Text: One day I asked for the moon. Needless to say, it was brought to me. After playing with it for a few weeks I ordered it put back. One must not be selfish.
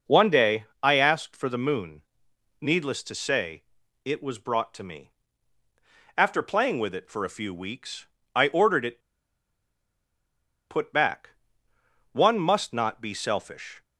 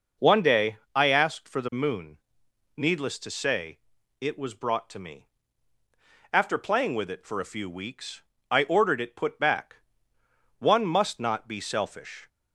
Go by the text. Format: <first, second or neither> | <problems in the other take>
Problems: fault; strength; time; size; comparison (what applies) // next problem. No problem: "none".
second | pauses between "day" and "I"; slight; at 0.6 s; 0.18 s long; slight in the second // pauses between "weeks" and "I"; slight; at 8.0 s; 0.26 s long; slight in the second // pauses between "it" and "put"; strong; at 9.0 s; 1.6 s long